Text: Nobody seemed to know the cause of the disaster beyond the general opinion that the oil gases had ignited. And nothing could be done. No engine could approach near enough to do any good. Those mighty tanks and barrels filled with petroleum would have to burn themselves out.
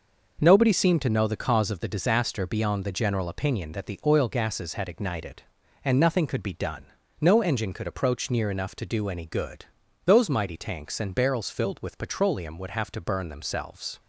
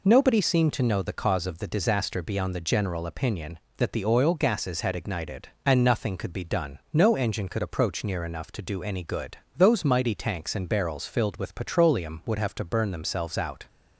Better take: second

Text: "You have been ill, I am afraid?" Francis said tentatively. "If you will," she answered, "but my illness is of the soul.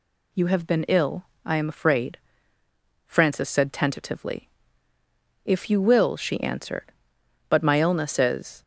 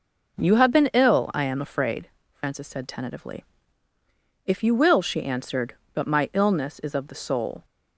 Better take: second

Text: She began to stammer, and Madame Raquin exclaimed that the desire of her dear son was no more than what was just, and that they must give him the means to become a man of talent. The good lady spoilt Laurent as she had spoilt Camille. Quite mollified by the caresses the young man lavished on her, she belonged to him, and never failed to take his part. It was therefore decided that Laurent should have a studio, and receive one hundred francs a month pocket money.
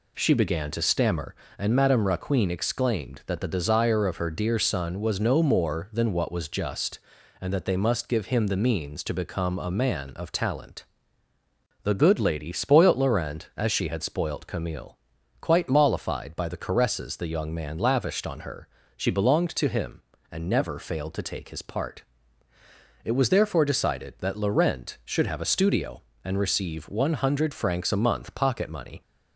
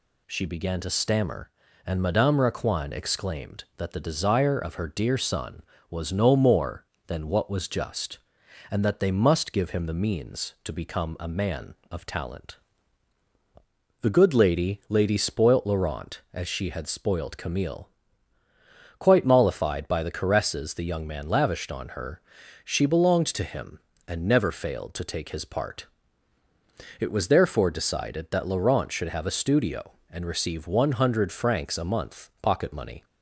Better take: first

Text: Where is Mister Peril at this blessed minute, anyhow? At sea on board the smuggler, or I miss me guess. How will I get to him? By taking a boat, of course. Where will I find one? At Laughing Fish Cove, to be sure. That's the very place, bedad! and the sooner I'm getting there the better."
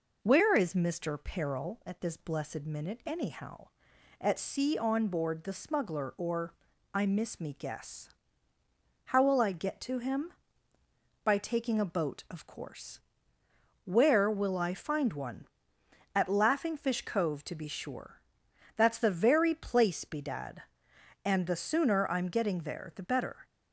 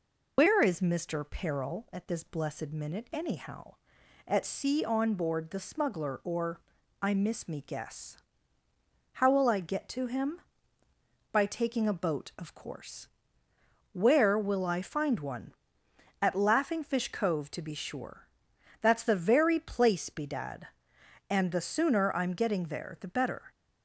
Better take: first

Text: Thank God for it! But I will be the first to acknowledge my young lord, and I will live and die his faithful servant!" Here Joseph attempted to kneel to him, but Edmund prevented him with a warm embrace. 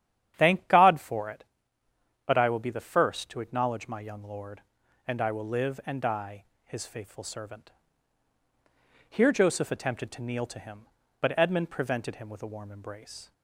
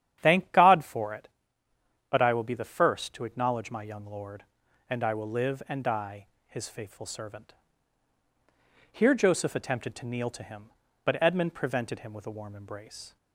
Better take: neither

